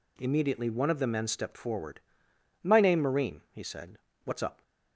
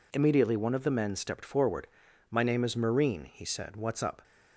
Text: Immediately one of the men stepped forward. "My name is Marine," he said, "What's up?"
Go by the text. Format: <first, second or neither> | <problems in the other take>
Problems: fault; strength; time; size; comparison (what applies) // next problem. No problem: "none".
second | skips "is"; at 2.9 s